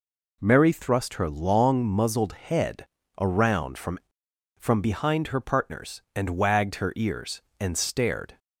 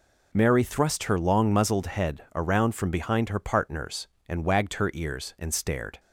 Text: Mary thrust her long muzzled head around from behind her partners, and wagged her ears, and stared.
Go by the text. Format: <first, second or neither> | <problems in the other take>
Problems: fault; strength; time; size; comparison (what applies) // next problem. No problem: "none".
second | pauses between "head" and "around"; slight; at 2.8 s; 0.34 s long // says "from" twice; at 4.5 s